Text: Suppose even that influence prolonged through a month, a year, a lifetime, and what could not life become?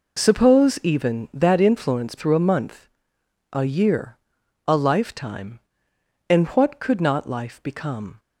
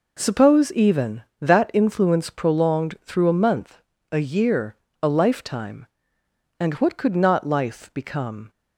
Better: second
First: skips "prolonged"; at 2.1 s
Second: none

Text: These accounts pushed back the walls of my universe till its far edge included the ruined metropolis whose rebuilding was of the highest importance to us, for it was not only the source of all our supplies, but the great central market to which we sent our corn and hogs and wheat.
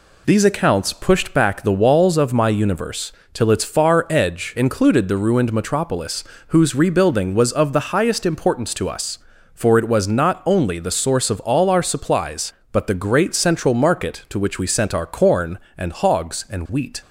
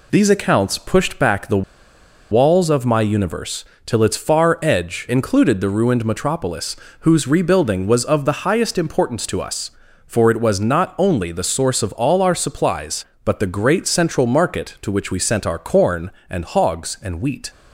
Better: first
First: pauses between "universe" and "till"; slight; at 3.1 s; 0.20 s long // pauses between "metropolis" and "whose"; slight; at 6.2 s; 0.24 s long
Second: pauses between "the" and "walls"; noticeable; at 1.6 s; 0.68 s long // pauses between "universe" and "till"; slight; at 3.6 s; 0.20 s long // pauses between "metropolis" and "whose"; slight; at 6.7 s; 0.24 s long

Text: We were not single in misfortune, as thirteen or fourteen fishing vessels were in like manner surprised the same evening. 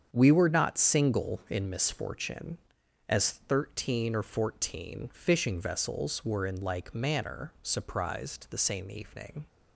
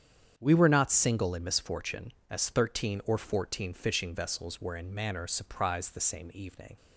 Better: first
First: starts louder than the rest; strong; until 1.1 s; 7.5 dB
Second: starts louder than the rest; strong; until 1.3 s; 8.5 dB // skips "like"; at 4.9 s

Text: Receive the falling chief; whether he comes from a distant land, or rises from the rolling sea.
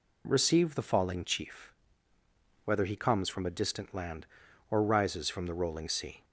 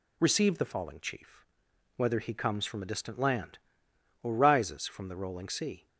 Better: neither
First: none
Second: none

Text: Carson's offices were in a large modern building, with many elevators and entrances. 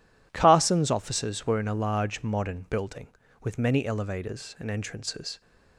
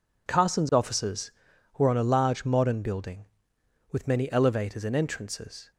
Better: first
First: none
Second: says "on" for "in"; at 1.8 s

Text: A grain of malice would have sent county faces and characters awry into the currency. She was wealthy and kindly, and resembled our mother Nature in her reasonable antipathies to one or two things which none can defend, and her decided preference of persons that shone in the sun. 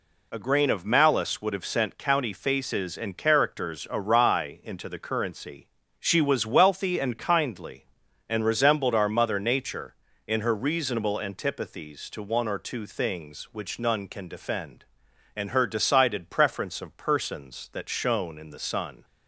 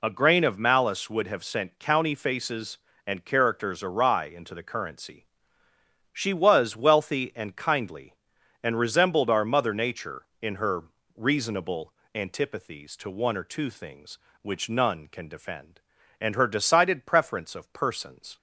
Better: first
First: none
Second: pauses between "her" and "reasonable"; slight; at 10.8 s; 0.32 s long // pauses between "reasonable" and "antipathies"; slight; at 11.9 s; 0.20 s long // stops before "that shone in the sun"; at 18.3 s

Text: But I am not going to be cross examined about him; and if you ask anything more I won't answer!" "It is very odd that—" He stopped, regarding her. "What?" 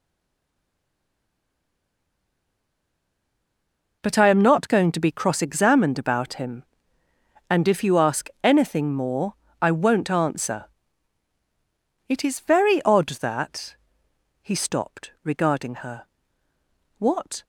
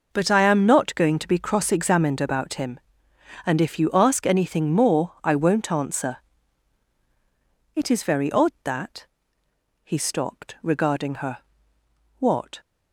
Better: second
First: stays silent before the first word; strong; until 4.0 s; 4.0 s long // pauses between "more" and "I"; slight; at 9.3 s; 0.28 s long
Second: none

